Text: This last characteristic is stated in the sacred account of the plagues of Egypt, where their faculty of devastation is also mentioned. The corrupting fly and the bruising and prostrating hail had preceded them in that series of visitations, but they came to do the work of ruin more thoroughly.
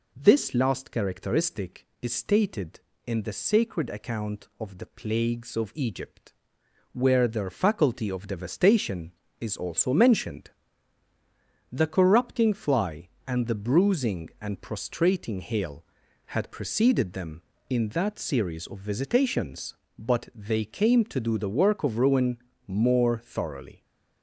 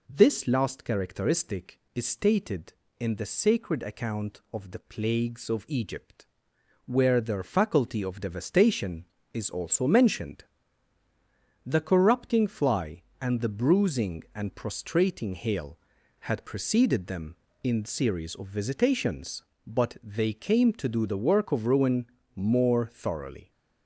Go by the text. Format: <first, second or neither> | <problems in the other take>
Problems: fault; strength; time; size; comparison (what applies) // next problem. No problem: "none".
first | skips "that"; at 17.8 s // pauses between "ruin" and "more"; slight; at 22.0 s; 0.30 s long; slight in the first